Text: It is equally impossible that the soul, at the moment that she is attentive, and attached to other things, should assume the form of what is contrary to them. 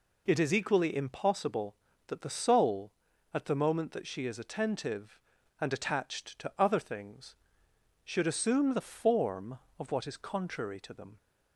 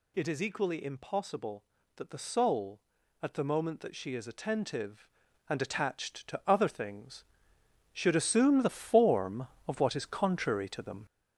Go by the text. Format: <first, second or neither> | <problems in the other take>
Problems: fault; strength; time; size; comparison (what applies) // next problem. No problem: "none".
first | gets louder; noticeable; throughout; 5 dB